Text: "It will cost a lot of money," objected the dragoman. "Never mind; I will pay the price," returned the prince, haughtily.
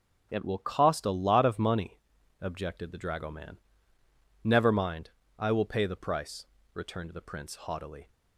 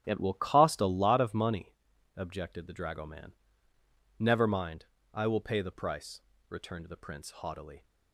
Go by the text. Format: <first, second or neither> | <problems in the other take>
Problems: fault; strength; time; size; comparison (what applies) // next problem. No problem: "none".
first | starts louder than the rest; strong; until 1.1 s; 9 dB